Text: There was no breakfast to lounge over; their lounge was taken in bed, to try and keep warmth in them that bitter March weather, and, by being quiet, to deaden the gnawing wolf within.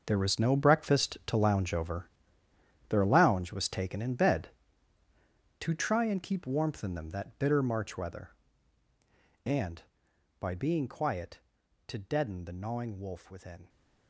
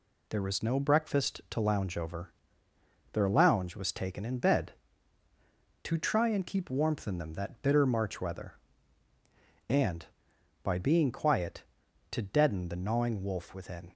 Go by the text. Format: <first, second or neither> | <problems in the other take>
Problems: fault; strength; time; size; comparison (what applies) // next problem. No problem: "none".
second | gets quieter; strong; throughout; 13.5 dB